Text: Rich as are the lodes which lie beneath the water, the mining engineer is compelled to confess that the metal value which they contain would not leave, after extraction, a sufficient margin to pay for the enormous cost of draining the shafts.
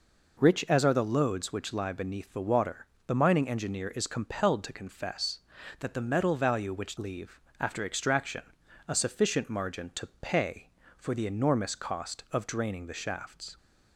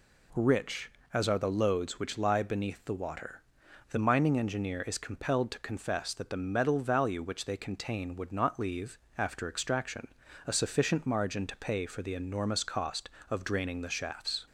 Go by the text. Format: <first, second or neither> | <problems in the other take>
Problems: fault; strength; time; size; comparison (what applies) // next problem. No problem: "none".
second | skips "they contain would not"; at 6.9 s